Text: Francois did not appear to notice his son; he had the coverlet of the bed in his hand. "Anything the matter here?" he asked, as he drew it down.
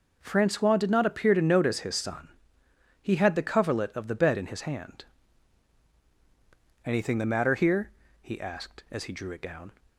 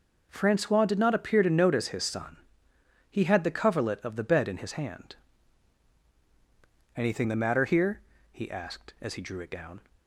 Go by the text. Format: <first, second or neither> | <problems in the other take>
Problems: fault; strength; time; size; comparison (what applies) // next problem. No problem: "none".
neither | none